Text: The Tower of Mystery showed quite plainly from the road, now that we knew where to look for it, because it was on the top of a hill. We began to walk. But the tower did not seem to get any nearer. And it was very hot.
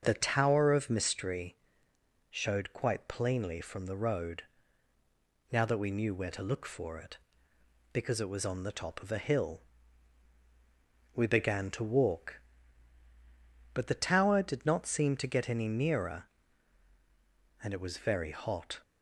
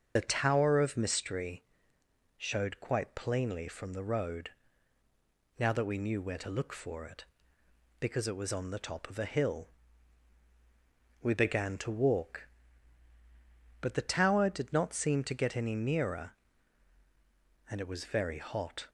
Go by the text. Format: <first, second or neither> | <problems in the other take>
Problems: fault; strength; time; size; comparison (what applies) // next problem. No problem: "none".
first | loses the start of "The"; at 0.1 s; 55 ms // starts louder than the rest; until 1.1 s; 6 dB; also in the first // pauses between "Mystery" and "showed"; noticeable; at 1.6 s; 0.74 s long; noticeable in the first